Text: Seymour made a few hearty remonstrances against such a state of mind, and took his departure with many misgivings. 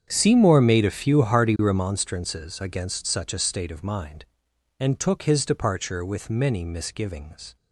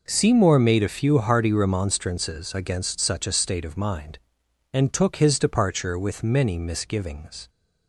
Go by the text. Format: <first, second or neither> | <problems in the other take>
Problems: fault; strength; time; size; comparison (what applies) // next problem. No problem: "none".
second | starts louder than the rest; strong; until 1.9 s; 8 dB